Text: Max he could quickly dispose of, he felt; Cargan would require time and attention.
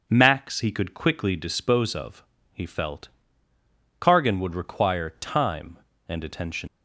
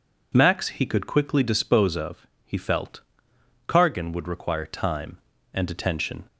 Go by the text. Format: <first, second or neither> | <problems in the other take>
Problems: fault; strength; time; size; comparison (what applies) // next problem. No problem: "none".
second | leaves "attention" unfinished; at 6.6 s; 115 ms